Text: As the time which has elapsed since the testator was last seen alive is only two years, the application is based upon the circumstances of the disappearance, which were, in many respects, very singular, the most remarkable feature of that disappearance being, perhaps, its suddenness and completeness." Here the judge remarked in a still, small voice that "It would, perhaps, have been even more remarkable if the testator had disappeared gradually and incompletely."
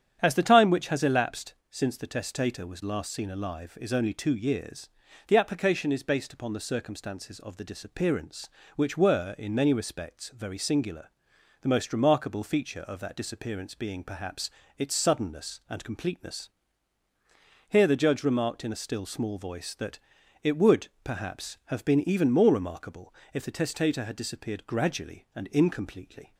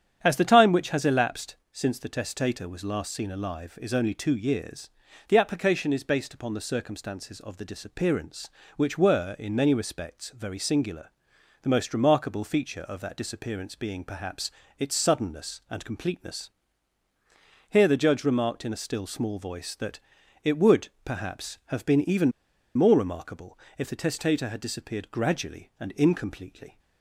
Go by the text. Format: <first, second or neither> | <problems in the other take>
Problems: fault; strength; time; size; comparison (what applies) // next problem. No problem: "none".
first | starts louder than the rest; strong; until 1.2 s; 9 dB; strong in the first // pauses between "elapsed" and "since"; slight; at 1.5 s; 0.18 s long; slight in the first // pauses between "that" and "It"; at 20.0 s; 0.42 s long; also in the first // pauses between "even" and "more"; at 22.3 s; 0.44 s long // pauses between "remarkable" and "if"; slight; at 23.5 s; 0.18 s long; slight in the first